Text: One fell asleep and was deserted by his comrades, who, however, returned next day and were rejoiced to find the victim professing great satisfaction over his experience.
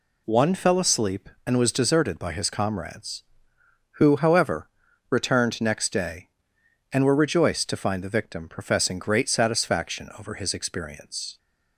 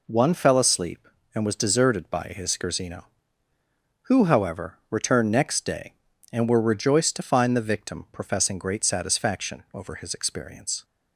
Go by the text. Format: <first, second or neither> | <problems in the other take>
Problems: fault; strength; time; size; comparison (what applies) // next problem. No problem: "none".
first | says "scherzino" for "comrades"; at 2.5 s